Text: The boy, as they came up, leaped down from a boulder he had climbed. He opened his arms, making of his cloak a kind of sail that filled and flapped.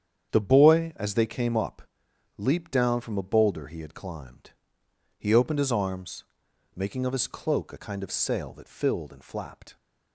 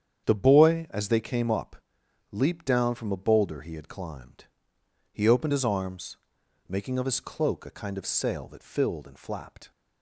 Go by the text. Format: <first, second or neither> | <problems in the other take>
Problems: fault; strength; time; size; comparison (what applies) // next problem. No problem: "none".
neither | starts louder than the rest; strong; the same in both